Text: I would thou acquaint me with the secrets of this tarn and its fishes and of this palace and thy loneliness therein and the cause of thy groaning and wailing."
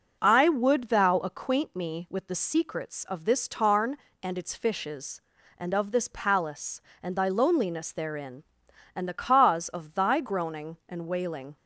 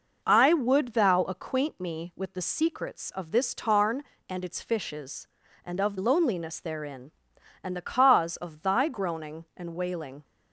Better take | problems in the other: first | skips "this palace and thy"; at 5.9 s

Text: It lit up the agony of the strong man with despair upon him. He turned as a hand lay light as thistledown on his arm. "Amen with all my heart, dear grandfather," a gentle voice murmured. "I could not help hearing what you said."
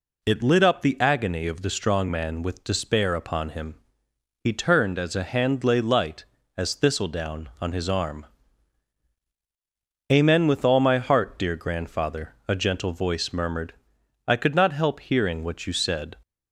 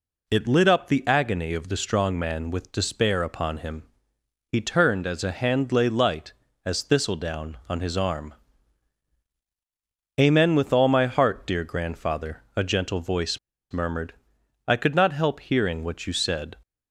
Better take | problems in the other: first | pauses between "voice" and "murmured"; slight; at 13.3 s; 0.33 s long

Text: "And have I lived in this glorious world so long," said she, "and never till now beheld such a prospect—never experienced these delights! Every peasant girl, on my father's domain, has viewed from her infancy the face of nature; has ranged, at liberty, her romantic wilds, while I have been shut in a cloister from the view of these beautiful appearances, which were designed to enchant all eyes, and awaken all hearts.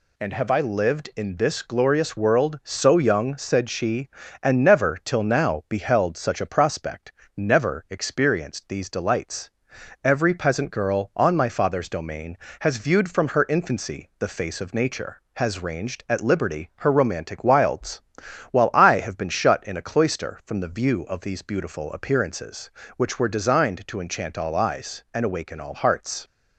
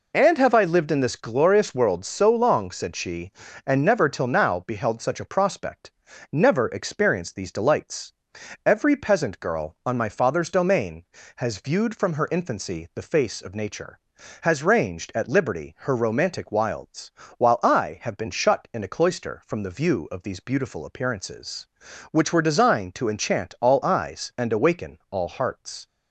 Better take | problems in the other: second | says "young" for "long"; at 2.9 s

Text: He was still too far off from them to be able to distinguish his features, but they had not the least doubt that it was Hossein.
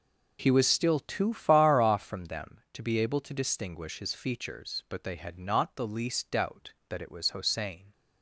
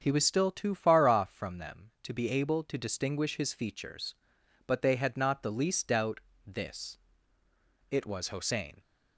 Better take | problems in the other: first | starts louder than the rest; until 1.0 s; 7 dB // says "this" for "that"; at 6.4 s

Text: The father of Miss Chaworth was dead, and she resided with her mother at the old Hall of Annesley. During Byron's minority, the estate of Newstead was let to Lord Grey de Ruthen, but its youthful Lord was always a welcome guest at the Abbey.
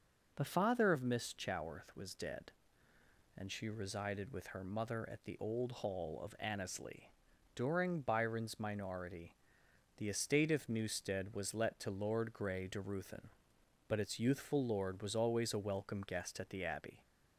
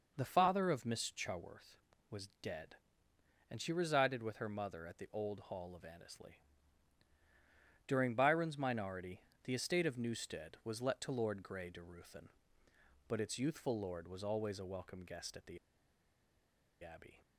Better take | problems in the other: first | pauses between "the" and "Abbey"; strong; at 15.5 s; 1.2 s long

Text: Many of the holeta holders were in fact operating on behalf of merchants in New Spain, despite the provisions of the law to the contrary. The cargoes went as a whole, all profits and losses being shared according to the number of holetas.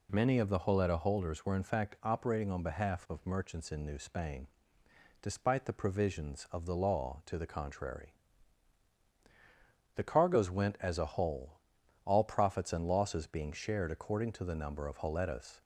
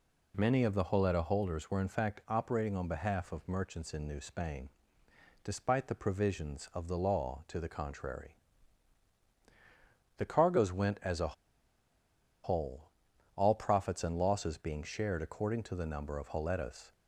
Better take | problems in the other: first | pauses between "a" and "whole"; at 11.3 s; 1.0 s long

